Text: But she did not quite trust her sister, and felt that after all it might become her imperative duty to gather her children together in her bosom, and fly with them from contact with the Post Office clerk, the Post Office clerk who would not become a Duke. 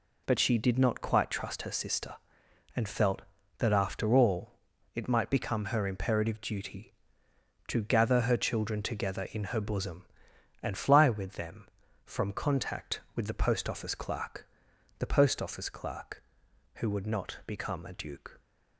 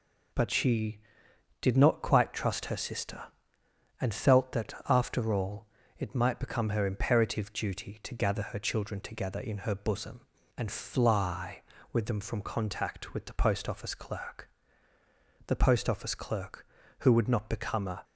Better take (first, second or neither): first